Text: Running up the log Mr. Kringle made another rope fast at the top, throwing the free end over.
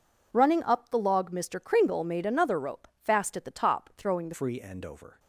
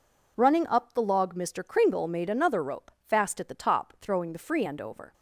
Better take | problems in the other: second | changes voice at "free"; from 4.3 s on; 0.8 s long

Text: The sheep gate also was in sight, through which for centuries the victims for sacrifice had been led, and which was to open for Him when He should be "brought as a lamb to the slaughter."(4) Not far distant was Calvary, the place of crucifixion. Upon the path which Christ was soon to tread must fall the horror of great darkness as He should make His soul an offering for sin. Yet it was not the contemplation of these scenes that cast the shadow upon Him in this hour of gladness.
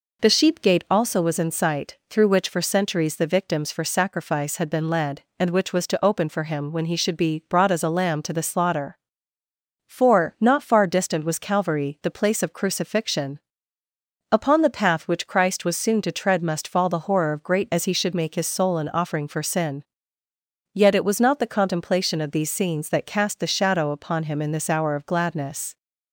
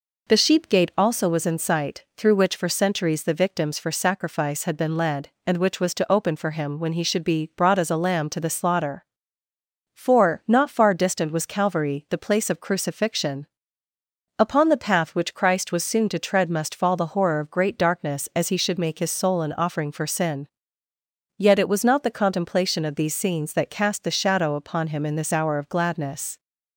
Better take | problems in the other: second | skips "darkness"; at 17.7 s

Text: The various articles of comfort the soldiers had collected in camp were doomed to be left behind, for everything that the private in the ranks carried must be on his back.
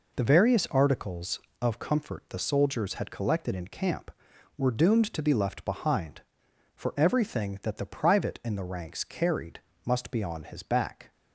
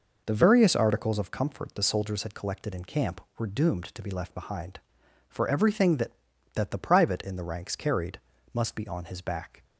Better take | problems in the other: first | says "that" twice; at 6.5 s // pauses between "carried" and "must"; slight; at 8.1 s; 0.34 s long; slight in the first

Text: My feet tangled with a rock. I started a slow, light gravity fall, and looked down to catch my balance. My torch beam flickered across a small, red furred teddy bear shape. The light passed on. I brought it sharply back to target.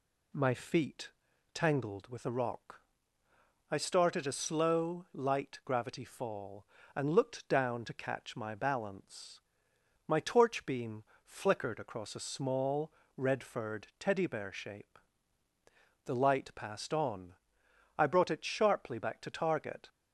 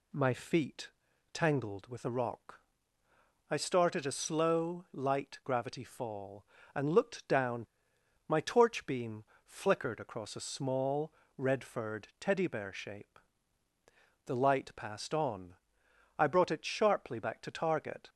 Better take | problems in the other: first | pauses between "feet" and "tangled"; at 0.8 s; 0.44 s long; also in the first // skips "to catch my balance"; at 7.9 s // pauses between "beam" and "flickered"; slight; at 9.2 s; 0.20 s long; slight in the first

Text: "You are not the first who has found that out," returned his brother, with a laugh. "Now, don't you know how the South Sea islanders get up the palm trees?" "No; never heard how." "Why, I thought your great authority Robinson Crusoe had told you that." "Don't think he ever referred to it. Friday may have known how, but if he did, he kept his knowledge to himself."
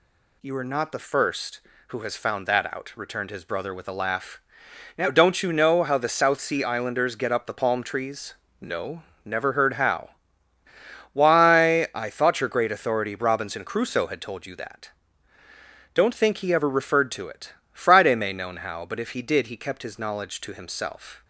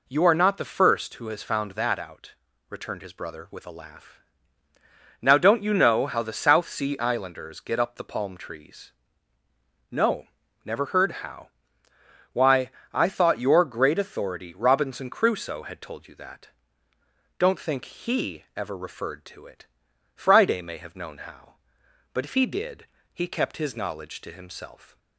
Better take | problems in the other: second | skips "have"; at 18.3 s

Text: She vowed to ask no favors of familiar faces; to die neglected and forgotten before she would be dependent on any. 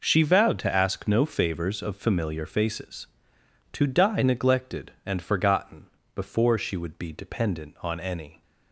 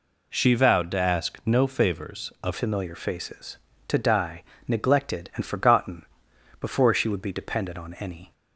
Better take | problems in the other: first | changes voice at "familiar"; from 2.5 s on; 5.8 s long // pauses between "die" and "neglected"; slight; at 4.4 s; 0.24 s long // pauses between "forgotten" and "before"; noticeable; at 6.0 s; 0.56 s long; slight in the first

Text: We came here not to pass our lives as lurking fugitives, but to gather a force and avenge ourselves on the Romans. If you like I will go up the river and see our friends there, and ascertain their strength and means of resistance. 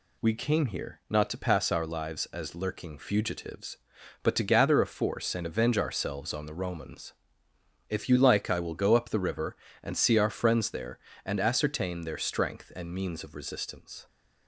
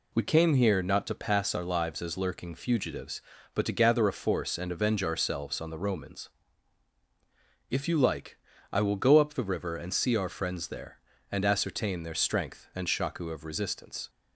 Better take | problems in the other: first | pauses between "like" and "I"; slight; at 8.3 s; 0.34 s long // says "shaku" for "means"; at 12.8 s

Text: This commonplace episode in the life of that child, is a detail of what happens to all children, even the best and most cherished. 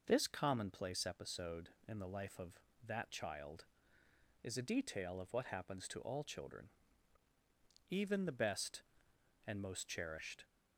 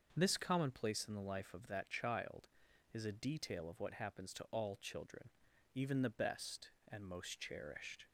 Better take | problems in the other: first | starts louder than the rest; until 1.1 s; 6.5 dB // skips "episode"; at 1.0 s

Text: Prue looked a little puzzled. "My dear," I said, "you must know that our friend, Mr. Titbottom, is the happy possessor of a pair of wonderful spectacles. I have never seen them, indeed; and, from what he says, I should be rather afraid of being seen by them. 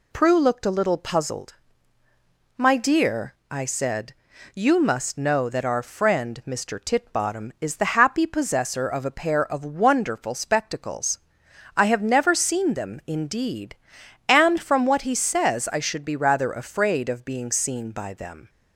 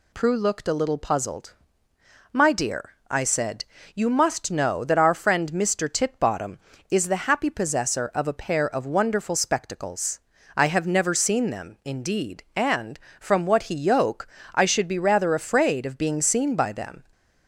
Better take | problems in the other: first | says "yoke" for "says"; at 13.7 s

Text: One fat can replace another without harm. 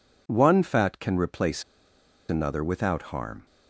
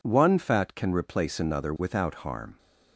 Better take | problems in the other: second | pauses between "replace" and "another"; noticeable; at 1.6 s; 0.66 s long

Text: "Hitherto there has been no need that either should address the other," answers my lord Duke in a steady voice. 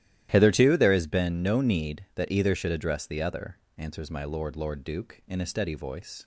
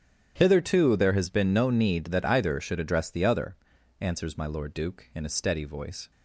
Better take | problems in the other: second | starts louder than the rest; strong; until 1.3 s; 13.5 dB; strong in the second // says "lord" twice; at 4.5 s

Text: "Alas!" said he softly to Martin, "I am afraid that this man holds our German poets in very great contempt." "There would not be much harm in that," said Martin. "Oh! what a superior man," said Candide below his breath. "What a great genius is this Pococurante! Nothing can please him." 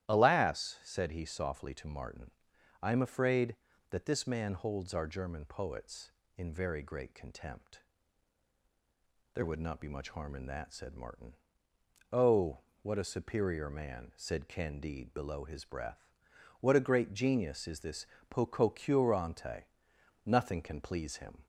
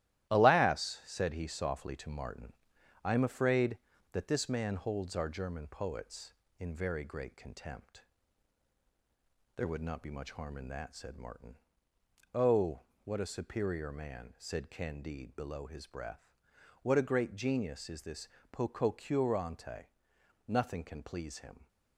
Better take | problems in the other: first | gets quieter; throughout; 6 dB // starts louder than the rest; strong; until 1.3 s; 14 dB; strong in the first // pauses between "this" and "Pococurante"; slight; at 18.2 s; 0.24 s long; slight in the first

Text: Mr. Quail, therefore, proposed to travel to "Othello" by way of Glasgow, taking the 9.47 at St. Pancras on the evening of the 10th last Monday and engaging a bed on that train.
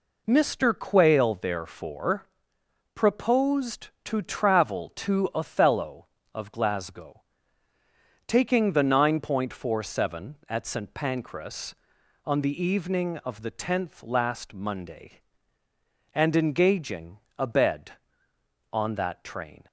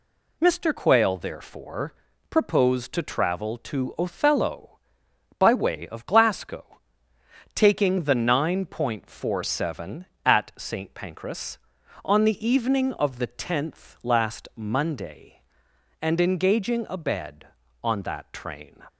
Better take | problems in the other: second | skips "by way"; at 6.1 s // pauses between "engaging" and "a"; slight; at 17.1 s; 0.18 s long

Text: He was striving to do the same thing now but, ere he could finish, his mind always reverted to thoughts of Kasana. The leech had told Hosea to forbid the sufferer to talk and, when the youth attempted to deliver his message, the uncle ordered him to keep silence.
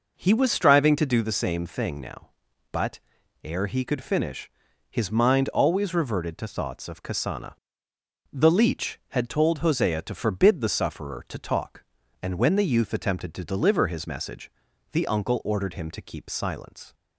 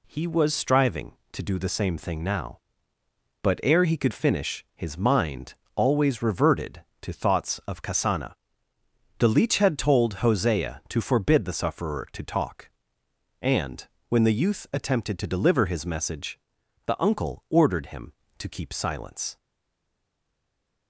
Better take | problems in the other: first | pauses between "mind" and "always"; slight; at 5.5 s; 0.22 s long // stays silent after the last word; noticeable; from 19.3 s on; 1.5 s long

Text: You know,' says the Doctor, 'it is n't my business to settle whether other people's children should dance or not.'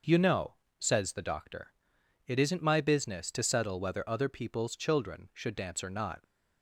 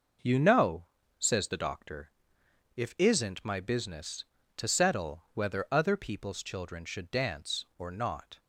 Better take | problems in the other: first | says "if" for "it"; at 2.7 s

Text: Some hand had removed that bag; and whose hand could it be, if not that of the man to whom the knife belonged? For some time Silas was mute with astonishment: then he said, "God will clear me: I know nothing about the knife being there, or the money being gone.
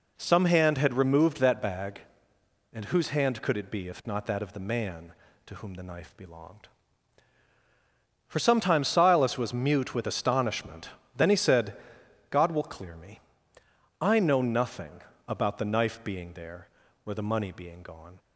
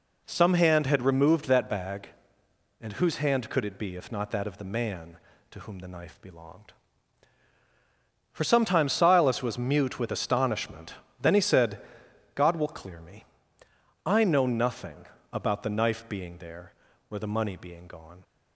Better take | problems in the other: neither | pauses between "nothing" and "about"; slight; the same in both

